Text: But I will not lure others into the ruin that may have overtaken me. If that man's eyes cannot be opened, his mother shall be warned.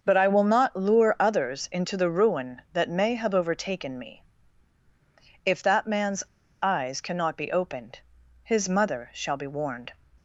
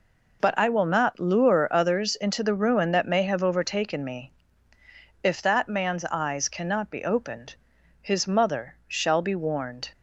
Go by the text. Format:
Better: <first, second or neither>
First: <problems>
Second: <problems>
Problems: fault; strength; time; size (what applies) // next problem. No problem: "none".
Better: second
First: starts louder than the rest; noticeable; until 1.0 s; 6 dB // pauses between "man's" and "eyes"; at 6.2 s; 0.38 s long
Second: none